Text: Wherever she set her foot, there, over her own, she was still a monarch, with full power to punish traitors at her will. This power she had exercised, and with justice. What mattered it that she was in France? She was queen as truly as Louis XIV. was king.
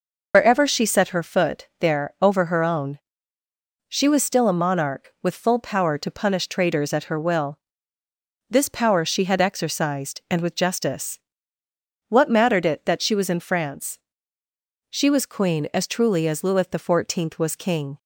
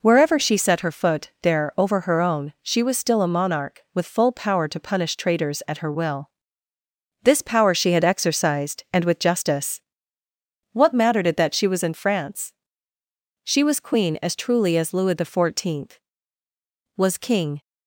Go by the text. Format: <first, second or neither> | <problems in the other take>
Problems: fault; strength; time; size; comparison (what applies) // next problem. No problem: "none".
second | loses the start of "Wherever"; at 0.3 s; 70 ms